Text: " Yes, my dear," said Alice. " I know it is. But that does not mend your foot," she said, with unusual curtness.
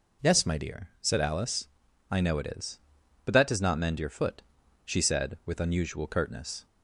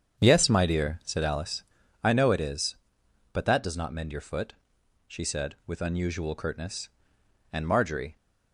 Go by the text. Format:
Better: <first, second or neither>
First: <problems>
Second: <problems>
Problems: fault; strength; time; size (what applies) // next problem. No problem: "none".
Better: first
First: none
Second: starts louder than the rest; strong; until 1.2 s; 8 dB // goes on to say "And Marjorie"; noticeable; from 7.5 s on; 0.64 s long